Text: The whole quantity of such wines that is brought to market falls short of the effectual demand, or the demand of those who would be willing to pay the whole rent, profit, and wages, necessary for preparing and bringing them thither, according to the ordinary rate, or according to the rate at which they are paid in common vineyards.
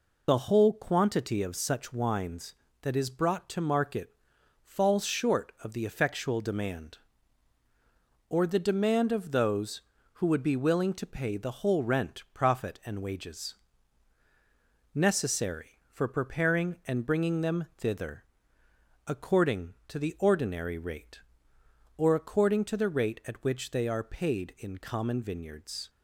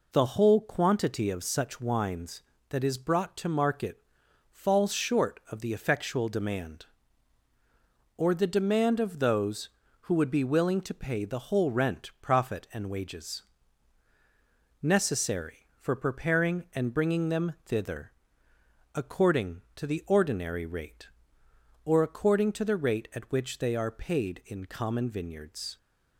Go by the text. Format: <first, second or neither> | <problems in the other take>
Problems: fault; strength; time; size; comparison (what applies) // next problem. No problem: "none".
second | loses the start of "The"; at 0.2 s; 25 ms // pauses between "market" and "falls"; noticeable; at 4.1 s; 0.54 s long; noticeable in the second